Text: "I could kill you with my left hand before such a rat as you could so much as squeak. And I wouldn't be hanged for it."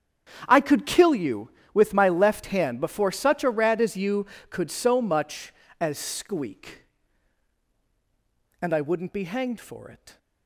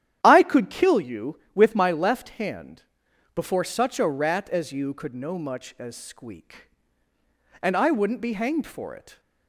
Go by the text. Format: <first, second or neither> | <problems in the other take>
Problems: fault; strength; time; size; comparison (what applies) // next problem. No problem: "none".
first | starts louder than the rest; strong; until 1.2 s; 11 dB; strong in the first // pauses between "hand" and "before"; noticeable; at 2.8 s; 0.52 s long // says "no" for "so"; at 5.1 s